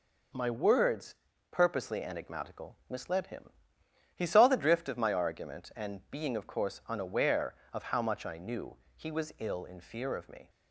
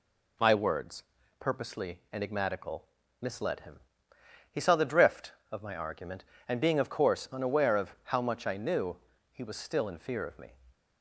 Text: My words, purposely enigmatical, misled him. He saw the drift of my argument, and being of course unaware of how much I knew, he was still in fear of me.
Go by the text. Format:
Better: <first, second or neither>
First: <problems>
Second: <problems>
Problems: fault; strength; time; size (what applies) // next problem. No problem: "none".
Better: second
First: says "ill" for "still"; at 9.3 s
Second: none